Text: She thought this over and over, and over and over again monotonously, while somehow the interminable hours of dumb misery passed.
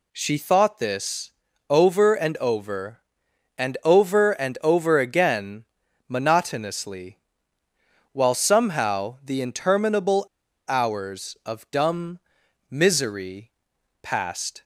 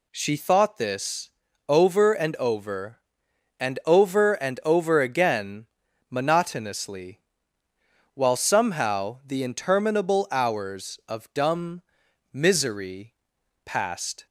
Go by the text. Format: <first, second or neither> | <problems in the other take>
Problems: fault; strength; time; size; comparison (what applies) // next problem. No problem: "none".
second | pauses between "this" and "over"; slight; at 1.3 s; 0.36 s long; slight in the second // pauses between "again" and "monotonously"; at 5.6 s; 0.44 s long; also in the second // pauses between "interminable" and "hours"; at 10.2 s; 0.41 s long // pauses between "dumb" and "misery"; noticeable; at 12.1 s; 0.52 s long; noticeable in the second // pauses between "misery" and "passed"; noticeable; at 13.5 s; 0.50 s long; noticeable in the second